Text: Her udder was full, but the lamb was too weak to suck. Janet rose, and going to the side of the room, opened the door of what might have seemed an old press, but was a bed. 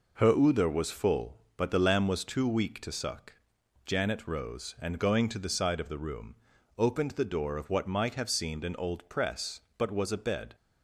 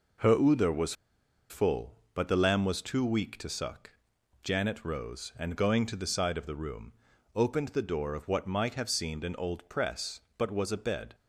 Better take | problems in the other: first | pauses between "was" and "full"; noticeable; at 0.9 s; 0.56 s long

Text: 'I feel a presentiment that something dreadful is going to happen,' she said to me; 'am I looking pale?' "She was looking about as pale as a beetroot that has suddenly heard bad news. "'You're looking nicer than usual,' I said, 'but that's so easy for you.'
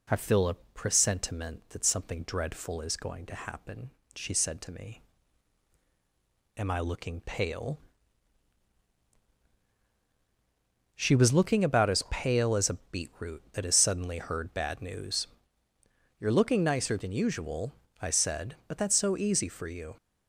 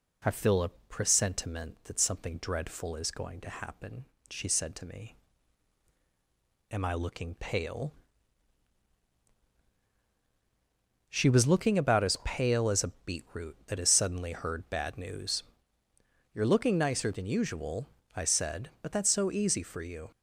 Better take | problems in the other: neither | none

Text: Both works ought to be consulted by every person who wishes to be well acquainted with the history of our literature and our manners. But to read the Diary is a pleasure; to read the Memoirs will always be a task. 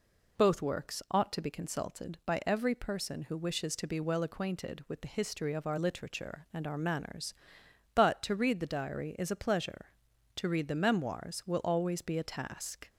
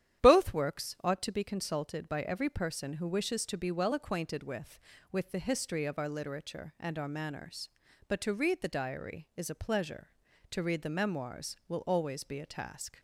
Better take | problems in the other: first | starts louder than the rest; strong; until 1.2 s; 10.5 dB // says "with" twice; at 5.1 s

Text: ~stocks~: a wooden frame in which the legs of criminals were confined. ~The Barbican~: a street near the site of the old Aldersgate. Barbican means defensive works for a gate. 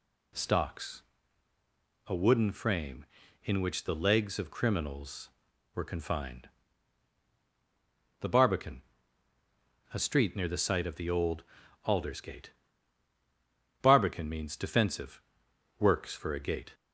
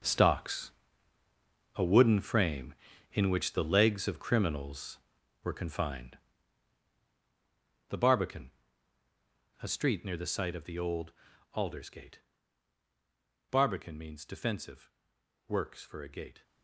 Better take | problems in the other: first | gets quieter; strong; throughout; 13 dB // pauses between "old" and "Aldersgate"; at 11.1 s; 0.40 s long; also in the first // pauses between "defensive" and "works"; noticeable; at 14.9 s; 0.56 s long; noticeable in the first

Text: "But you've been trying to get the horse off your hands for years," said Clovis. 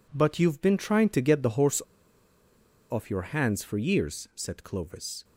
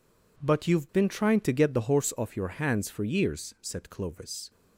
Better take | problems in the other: second | pauses between "horse" and "off"; at 1.8 s; 1.0 s long

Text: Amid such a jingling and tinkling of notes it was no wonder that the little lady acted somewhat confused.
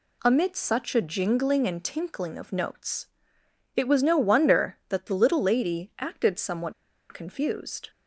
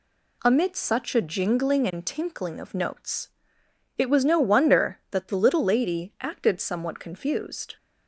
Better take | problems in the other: second | pauses between "notes" and "it"; noticeable; at 3.0 s; 0.70 s long; noticeable in the second // pauses between "somewhat" and "confused"; at 6.7 s; 0.38 s long

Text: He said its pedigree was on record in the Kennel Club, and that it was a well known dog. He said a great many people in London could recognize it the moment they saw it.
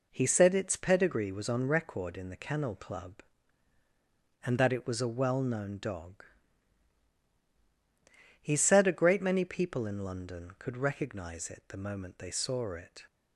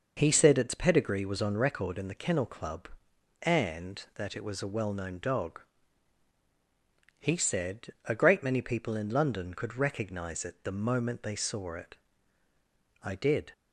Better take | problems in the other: first | pauses between "said" and "a"; slight; at 7.8 s; 0.18 s long // goes on to say "I did"; from 13.0 s on; 0.50 s long

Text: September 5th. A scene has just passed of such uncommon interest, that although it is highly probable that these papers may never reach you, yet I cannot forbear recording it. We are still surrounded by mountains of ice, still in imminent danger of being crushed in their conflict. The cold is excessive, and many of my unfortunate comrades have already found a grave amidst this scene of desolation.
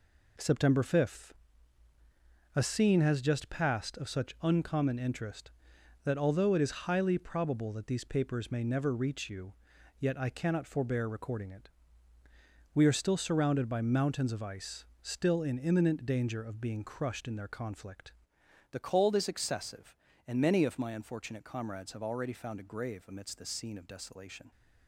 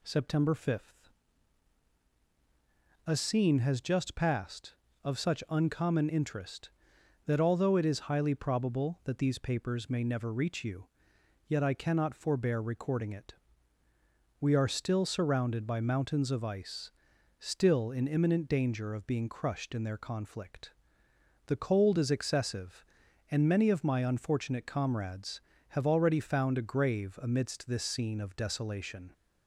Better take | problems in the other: second | changes voice at "The"; from 18.7 s on; 5.8 s long

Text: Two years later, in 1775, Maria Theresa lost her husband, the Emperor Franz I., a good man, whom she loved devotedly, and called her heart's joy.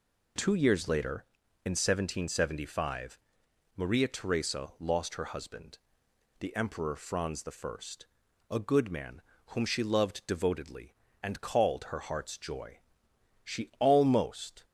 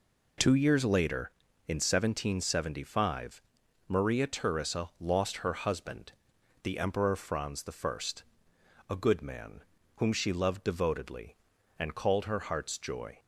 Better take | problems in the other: second | goes on to say "She almost"; noticeable; from 13.4 s on; 1.2 s long

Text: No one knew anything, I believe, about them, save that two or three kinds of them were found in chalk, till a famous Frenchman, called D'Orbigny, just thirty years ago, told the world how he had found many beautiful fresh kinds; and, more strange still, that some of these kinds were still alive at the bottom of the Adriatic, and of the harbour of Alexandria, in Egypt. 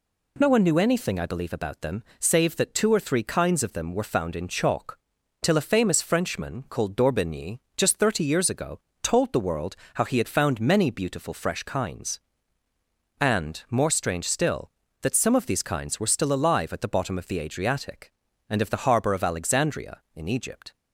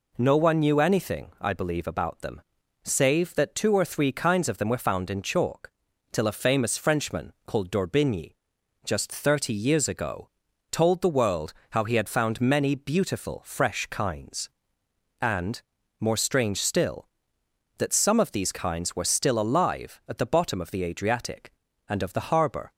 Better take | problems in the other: first | pauses between "world" and "how"; slight; at 11.5 s; 0.20 s long; slight in the first // stops before "of Alexandria in Egypt"; at 22.7 s

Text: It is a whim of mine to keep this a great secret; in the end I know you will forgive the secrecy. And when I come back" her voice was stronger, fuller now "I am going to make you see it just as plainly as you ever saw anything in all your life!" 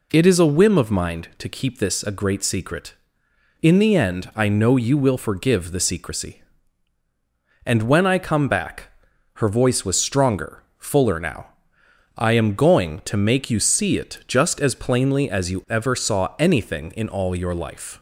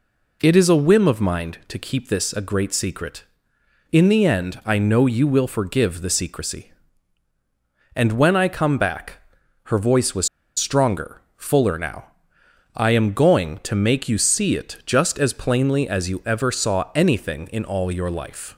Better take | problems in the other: first | pauses between "back" and "her"; noticeable; at 9.1 s; 0.46 s long; noticeable in the first // pauses between "was" and "stronger"; slight; at 10.2 s; 0.29 s long // pauses between "now" and "I"; noticeable; at 12.0 s; 0.66 s long; noticeable in the first

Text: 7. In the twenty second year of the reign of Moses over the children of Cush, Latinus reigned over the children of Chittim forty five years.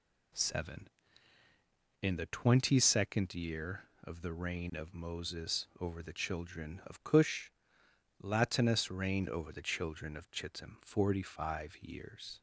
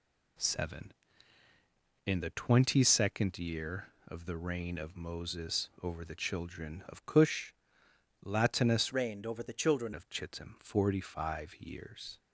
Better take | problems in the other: first | changes voice from "reigned" to "children"; from 8.9 to 9.9 s; 1.0 s long

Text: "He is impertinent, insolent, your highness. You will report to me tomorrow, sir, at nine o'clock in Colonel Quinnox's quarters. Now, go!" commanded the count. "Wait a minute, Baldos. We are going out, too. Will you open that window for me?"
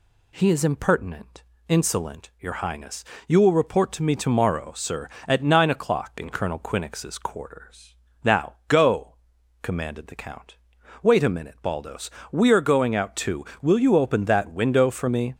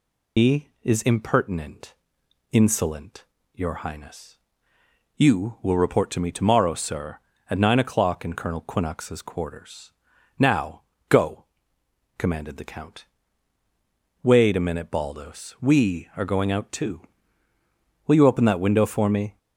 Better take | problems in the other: first | loses the start of "He"; at 0.3 s; 145 ms

